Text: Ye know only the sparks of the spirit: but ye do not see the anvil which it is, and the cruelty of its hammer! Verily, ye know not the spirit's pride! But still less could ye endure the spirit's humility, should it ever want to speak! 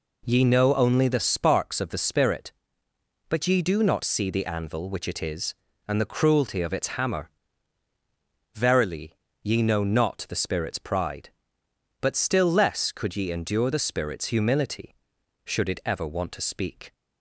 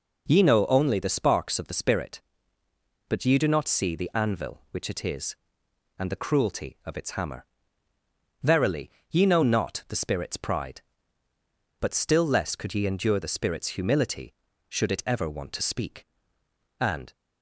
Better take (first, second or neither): first